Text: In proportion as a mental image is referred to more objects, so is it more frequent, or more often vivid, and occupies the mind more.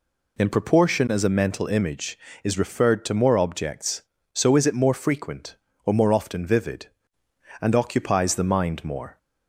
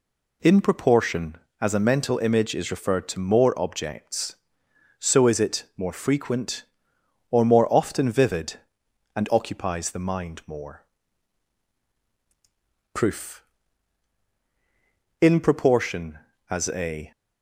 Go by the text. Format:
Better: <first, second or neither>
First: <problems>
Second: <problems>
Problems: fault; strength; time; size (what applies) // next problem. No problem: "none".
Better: first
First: none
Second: goes on to say "Proof In proportion as a"; strong; from 12.9 s on; 4.1 s long